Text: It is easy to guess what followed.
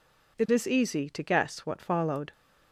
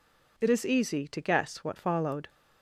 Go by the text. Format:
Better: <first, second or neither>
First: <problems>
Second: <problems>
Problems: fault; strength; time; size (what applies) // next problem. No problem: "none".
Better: neither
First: none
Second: none